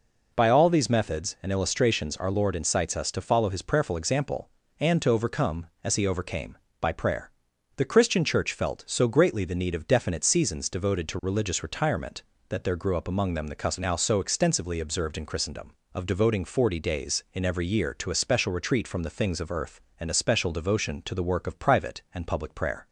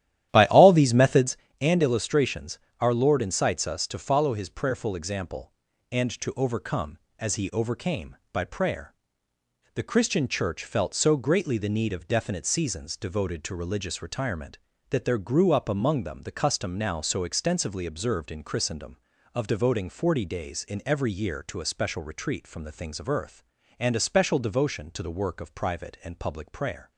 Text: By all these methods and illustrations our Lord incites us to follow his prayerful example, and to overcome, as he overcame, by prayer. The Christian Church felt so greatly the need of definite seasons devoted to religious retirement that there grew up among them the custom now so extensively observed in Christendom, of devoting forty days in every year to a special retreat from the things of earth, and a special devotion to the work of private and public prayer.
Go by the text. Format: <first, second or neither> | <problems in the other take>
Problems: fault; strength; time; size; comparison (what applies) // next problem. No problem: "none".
first | starts louder than the rest; strong; until 1.4 s; 12 dB // pauses between "illustrations" and "our"; slight; at 2.5 s; 0.20 s long